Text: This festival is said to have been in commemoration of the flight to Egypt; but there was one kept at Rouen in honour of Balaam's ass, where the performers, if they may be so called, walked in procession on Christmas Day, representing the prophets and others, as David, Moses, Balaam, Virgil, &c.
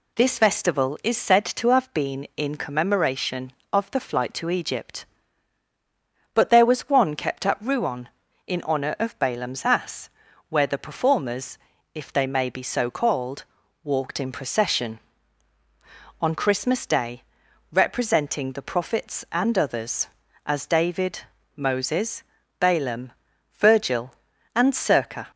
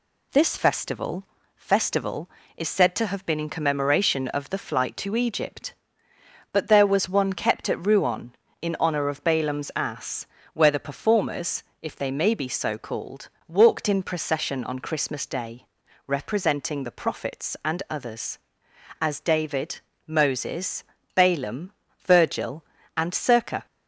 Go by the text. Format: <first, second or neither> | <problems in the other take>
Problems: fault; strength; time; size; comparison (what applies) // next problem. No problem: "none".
first | says "festival" twice; at 1.5 s